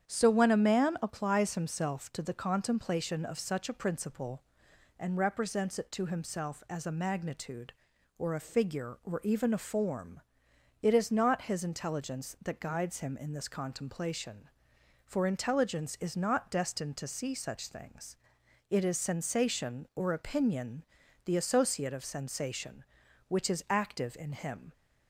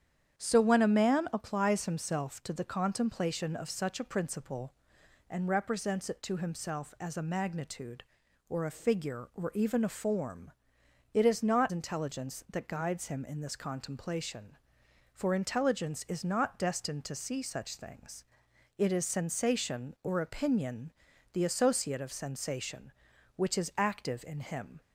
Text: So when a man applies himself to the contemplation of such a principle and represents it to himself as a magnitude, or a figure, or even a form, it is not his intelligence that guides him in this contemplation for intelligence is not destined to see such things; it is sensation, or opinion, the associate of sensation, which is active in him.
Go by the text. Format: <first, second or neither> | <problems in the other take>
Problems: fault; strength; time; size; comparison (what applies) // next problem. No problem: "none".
first | starts louder than the rest; strong; until 1.4 s; 9 dB; strong in the first // skips "his"; at 11.7 s